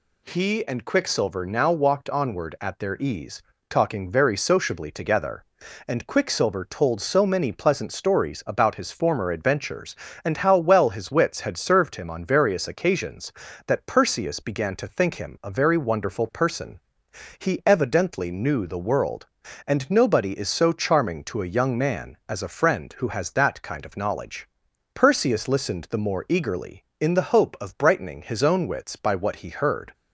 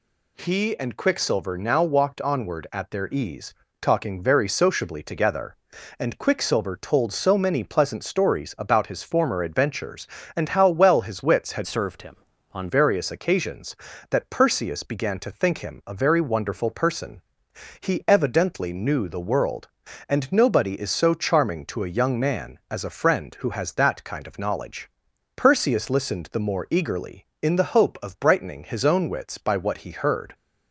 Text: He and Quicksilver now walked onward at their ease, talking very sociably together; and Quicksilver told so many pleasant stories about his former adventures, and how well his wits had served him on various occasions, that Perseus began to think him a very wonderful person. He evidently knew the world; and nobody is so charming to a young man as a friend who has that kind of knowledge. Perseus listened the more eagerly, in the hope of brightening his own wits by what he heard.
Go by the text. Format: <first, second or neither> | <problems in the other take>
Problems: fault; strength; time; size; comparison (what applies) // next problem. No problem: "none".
first | changes voice from "served" to "on"; from 11.6 to 12.6 s; 1.0 s long